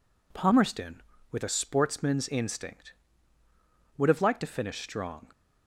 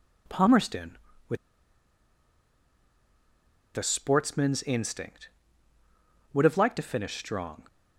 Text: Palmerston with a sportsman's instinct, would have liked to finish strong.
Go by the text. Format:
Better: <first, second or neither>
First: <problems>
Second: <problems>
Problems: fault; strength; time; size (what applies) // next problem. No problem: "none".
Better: first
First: none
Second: pauses between "with" and "a"; strong; at 1.3 s; 2.3 s long